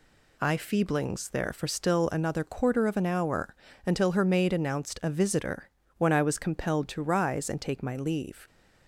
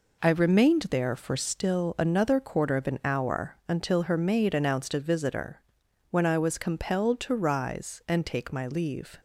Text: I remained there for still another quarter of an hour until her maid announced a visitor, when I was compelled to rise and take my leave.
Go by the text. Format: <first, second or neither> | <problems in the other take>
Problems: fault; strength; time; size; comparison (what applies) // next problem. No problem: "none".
second | says "feeblings" for "remained"; at 0.5 s // pauses between "hour" and "until"; slight; at 3.5 s; 0.32 s long